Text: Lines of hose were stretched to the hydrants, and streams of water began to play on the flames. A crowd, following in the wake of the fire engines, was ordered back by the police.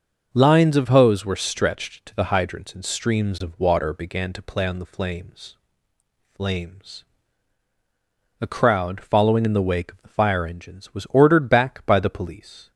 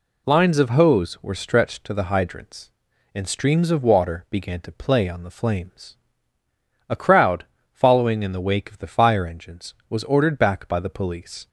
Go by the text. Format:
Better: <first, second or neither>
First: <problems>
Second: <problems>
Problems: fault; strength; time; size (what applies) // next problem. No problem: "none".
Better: second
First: starts louder than the rest; noticeable; until 1.3 s; 6 dB // says "flames" twice; at 6.3 s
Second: none